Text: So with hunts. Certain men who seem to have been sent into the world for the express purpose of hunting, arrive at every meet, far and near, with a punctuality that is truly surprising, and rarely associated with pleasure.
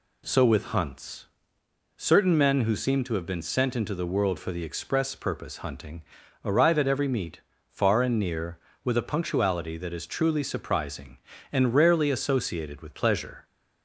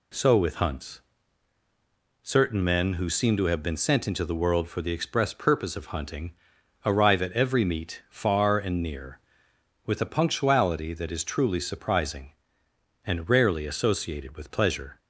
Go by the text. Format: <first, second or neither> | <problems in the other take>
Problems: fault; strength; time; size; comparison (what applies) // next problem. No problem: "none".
second | skips "of"; at 5.5 s